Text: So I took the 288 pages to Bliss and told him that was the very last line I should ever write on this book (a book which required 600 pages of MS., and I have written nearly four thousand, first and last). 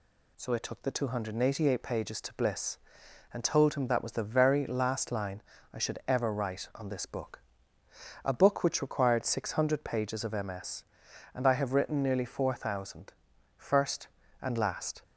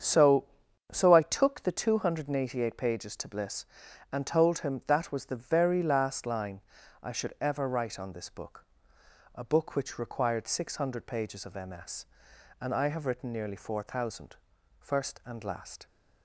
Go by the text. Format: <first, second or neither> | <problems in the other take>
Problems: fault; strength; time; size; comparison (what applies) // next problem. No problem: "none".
first | starts louder than the rest; strong; until 1.4 s; 8 dB // says "So" twice; at 0.9 s // pauses between "line" and "I"; at 6.5 s; 0.44 s long; slight in the first